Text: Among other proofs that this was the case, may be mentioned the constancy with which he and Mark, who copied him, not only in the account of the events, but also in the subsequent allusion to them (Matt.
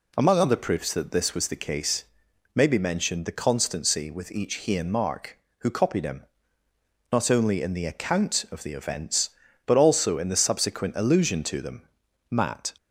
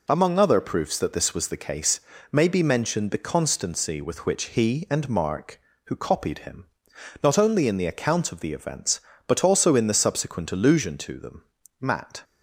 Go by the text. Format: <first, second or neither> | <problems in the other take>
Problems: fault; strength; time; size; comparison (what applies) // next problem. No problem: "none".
second | says "each" for "which"; at 4.3 s